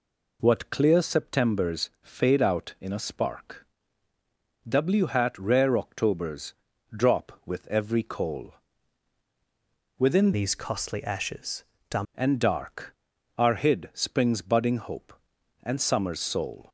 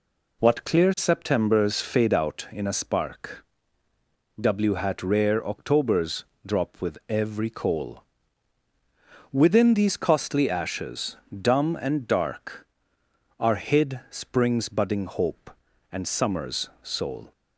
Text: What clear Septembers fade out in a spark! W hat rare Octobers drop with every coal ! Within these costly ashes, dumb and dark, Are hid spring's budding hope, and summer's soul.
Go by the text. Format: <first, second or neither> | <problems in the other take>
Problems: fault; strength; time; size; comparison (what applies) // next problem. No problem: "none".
second | pauses between "Octobers" and "drop"; at 6.5 s; 0.42 s long; slight in the second // changes voice from "these" to "dumb"; from 10.3 to 12.0 s; 1.7 s long